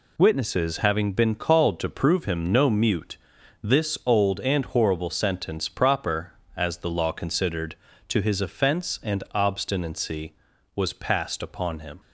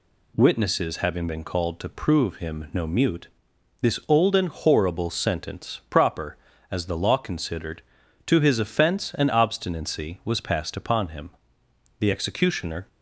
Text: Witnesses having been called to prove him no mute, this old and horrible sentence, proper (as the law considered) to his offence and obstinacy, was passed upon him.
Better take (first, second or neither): first